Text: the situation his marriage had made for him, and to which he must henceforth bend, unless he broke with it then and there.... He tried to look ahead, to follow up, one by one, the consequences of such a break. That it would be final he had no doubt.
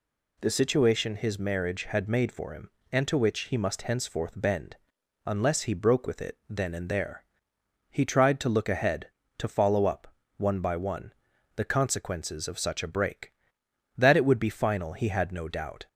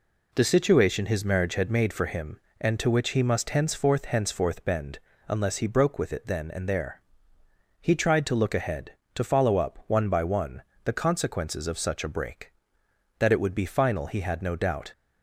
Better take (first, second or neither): first